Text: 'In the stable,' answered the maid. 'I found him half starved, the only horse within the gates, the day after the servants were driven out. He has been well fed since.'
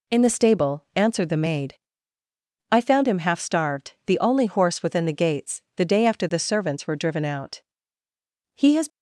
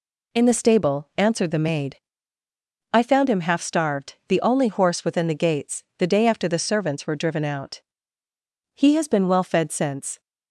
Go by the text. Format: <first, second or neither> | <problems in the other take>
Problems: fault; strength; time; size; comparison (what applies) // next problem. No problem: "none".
second | stops before "been well fed since"; at 8.8 s